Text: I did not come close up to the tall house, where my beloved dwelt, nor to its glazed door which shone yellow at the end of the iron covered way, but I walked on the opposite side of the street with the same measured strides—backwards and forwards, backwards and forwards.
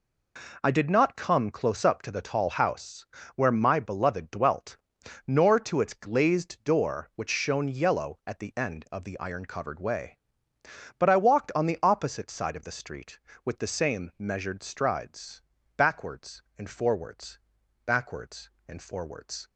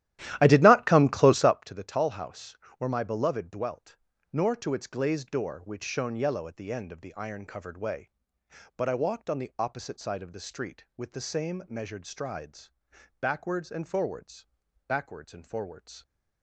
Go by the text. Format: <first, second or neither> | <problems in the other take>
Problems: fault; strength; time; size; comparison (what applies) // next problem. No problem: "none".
first | starts louder than the rest; strong; until 1.6 s; 13.5 dB